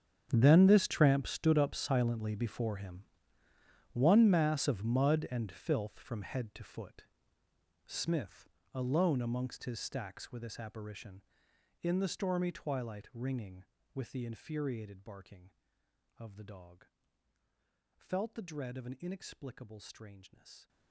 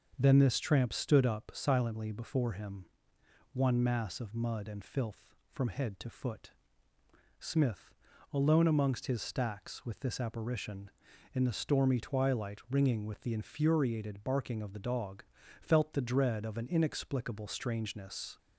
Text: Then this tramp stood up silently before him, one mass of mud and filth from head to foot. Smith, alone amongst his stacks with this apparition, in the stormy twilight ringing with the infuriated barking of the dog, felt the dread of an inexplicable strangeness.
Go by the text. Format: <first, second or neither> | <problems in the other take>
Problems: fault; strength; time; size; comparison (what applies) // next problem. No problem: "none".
second | gets quieter; strong; throughout; 18.5 dB // starts louder than the rest; strong; until 1.3 s; 8 dB; also in the second